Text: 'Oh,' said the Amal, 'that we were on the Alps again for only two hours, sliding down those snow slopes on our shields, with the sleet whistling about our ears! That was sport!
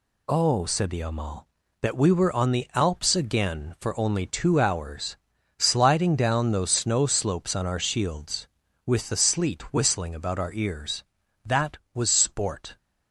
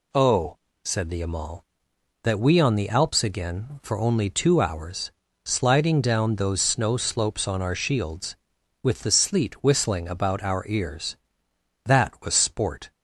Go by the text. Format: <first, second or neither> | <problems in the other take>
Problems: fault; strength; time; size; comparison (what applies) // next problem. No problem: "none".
first | skips "were"; at 2.5 s